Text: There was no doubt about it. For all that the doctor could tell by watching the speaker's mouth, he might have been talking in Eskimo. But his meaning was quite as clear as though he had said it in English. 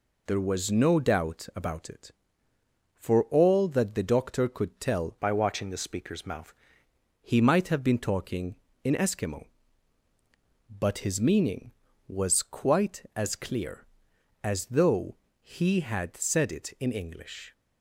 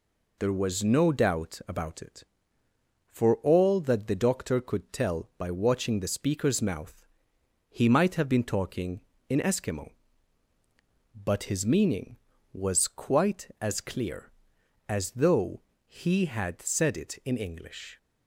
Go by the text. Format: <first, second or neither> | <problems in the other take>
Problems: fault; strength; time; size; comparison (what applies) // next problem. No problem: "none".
second | changes voice from "by" to "mouth"; from 5.1 to 6.5 s; 1.4 s long // pauses between "though" and "he"; slight; at 15.1 s; 0.26 s long; slight in the second